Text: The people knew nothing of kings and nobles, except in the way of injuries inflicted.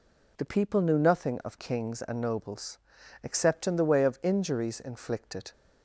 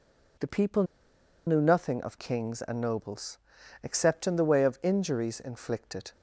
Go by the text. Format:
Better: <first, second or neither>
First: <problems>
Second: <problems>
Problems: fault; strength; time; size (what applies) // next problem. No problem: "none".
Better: first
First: none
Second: pauses between "people" and "knew"; noticeable; at 0.8 s; 0.63 s long